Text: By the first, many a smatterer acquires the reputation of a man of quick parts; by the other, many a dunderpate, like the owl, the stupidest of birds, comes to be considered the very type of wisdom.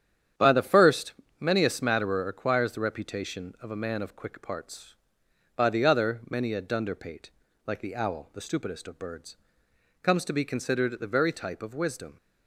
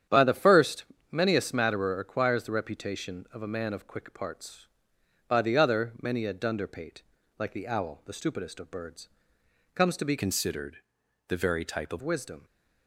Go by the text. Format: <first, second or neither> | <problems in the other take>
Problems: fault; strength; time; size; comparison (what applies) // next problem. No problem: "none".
first | starts louder than the rest; strong; until 1.3 s; 9 dB; strong in the first // changes voice from "considered" to "of"; from 10.1 to 12.0 s; 1.9 s long // pauses between "considered" and "the"; noticeable; at 10.7 s; 0.50 s long